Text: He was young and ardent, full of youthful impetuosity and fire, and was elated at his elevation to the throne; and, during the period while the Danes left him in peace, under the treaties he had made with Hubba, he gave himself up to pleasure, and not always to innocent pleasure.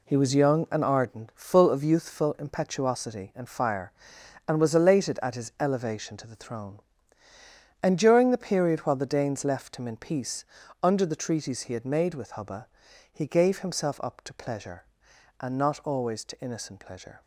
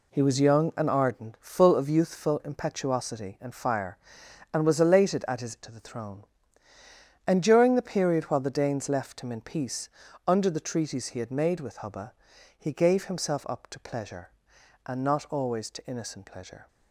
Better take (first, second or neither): first